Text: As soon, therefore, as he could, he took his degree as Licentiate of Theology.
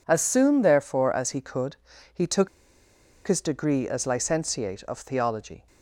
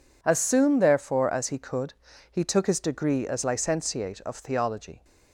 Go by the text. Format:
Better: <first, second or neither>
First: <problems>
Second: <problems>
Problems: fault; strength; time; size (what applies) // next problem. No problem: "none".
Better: second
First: pauses between "took" and "his"; noticeable; at 2.4 s; 0.78 s long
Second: none